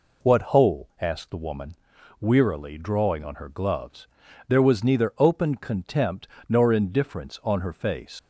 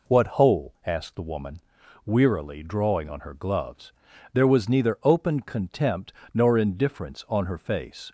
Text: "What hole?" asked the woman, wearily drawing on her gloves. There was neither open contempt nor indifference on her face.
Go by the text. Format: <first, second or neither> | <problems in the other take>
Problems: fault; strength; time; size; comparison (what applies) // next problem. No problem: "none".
second | pauses between "contempt" and "nor"; slight; at 6.2 s; 0.20 s long; slight in the second // leaves "face" unfinished; at 8.1 s; 75 ms